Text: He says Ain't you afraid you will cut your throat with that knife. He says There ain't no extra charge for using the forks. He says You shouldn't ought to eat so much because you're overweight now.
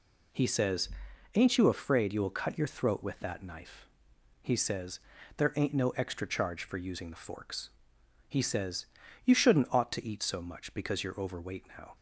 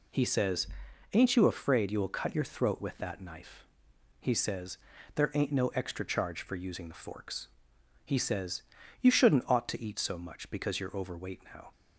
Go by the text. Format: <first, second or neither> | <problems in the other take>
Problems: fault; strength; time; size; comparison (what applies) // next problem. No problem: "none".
neither | pauses between "says" and "Ain't"; noticeable; the same in both // pauses between "says" and "There"; the same in both // pauses between "says" and "You"; the same in both